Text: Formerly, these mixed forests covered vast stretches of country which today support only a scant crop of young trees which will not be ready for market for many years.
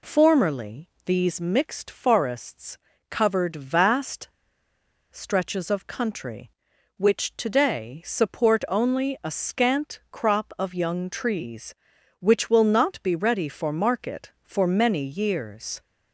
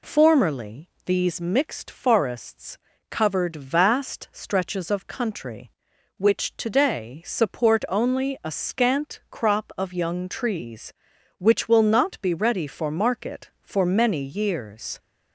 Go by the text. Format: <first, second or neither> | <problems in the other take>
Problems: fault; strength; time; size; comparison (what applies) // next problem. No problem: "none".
second | pauses between "forests" and "covered"; slight; at 2.7 s; 0.32 s long; slight in the second // pauses between "vast" and "stretches"; noticeable; at 4.2 s; 0.83 s long